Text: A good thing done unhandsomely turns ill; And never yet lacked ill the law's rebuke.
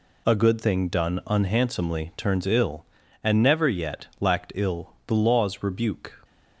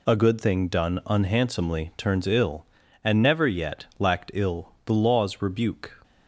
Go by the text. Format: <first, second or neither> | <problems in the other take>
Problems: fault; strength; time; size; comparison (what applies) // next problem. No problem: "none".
neither | none